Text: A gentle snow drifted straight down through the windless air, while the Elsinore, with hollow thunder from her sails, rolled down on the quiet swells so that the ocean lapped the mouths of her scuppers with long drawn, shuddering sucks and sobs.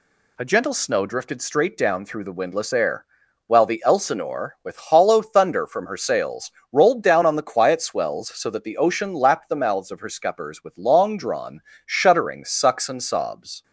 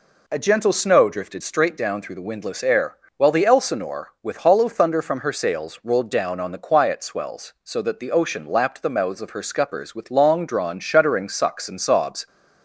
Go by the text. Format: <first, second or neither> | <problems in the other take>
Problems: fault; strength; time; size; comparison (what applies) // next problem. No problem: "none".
neither | none